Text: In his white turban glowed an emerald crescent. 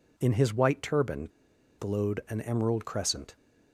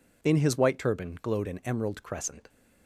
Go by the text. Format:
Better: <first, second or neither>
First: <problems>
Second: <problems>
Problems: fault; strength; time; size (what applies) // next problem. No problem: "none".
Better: second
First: pauses between "turban" and "glowed"; noticeable; at 1.2 s; 0.49 s long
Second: none